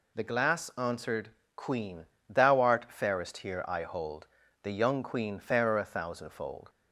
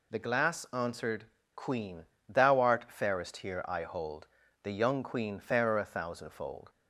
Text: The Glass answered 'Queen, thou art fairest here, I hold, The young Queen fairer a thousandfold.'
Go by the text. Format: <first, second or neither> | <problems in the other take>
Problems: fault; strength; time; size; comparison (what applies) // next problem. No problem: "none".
neither | pauses between "answered" and "Queen"; slight; the same in both